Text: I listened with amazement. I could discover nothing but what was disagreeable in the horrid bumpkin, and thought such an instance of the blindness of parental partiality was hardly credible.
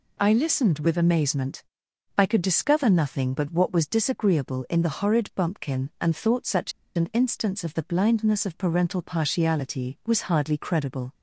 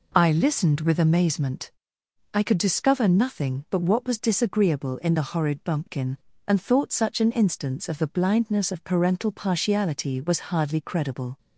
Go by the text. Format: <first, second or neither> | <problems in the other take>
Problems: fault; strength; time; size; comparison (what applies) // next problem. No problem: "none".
second | pauses between "such" and "an"; slight; at 6.7 s; 0.25 s long